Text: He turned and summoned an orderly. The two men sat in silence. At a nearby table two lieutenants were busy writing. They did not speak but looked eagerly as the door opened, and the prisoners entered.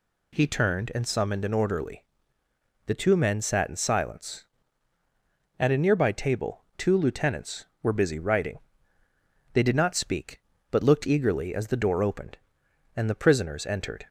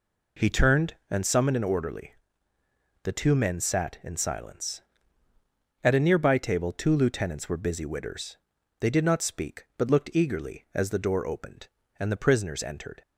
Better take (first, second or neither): first